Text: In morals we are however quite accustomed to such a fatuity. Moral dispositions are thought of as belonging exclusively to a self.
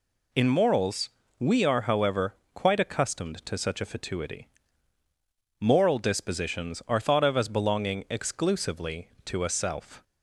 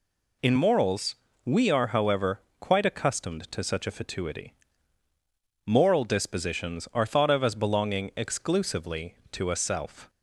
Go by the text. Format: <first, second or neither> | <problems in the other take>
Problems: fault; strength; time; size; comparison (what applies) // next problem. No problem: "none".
neither | pauses between "morals" and "we"; slight; the same in both // pauses between "however" and "quite"; slight; the same in both